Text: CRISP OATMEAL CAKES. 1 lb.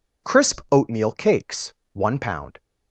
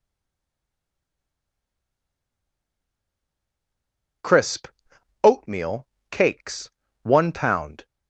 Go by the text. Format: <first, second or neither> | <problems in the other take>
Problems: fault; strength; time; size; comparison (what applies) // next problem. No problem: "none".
first | stays silent before the first word; strong; until 4.2 s; 4.2 s long // pauses between "CRISP" and "OATMEAL"; noticeable; at 4.6 s; 0.56 s long // pauses between "OATMEAL" and "CAKES"; slight; at 5.8 s; 0.24 s long